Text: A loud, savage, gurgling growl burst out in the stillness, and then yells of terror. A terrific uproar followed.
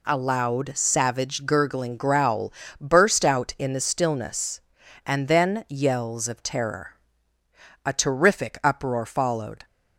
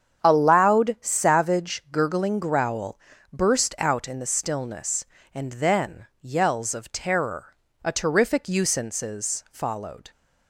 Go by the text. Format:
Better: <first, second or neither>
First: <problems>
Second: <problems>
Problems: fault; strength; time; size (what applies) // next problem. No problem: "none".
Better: first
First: pauses between "growl" and "burst"; slight; at 2.5 s; 0.28 s long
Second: starts louder than the rest; strong; until 1.2 s; 8 dB // pauses between "growl" and "burst"; slight; at 2.9 s; 0.32 s long // says "usances" for "uproar"; at 8.4 s